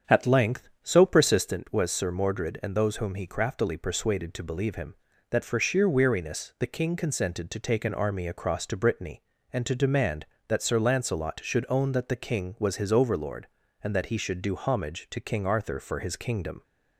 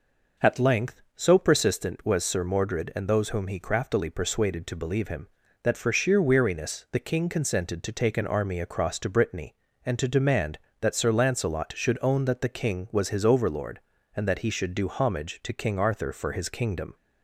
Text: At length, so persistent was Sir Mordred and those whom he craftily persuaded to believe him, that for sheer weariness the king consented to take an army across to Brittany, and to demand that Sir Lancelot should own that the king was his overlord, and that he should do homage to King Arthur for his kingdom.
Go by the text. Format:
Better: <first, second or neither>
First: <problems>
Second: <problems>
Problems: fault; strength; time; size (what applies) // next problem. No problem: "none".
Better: second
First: starts louder than the rest; strong; until 1.6 s; 7.5 dB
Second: none